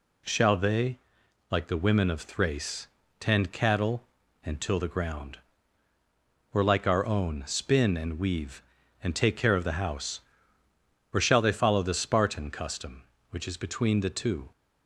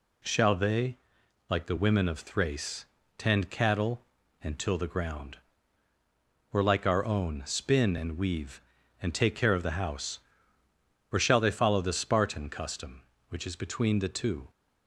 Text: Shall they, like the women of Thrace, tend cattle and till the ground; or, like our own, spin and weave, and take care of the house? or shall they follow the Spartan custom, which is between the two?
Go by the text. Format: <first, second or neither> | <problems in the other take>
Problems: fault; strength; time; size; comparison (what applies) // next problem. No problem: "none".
neither | none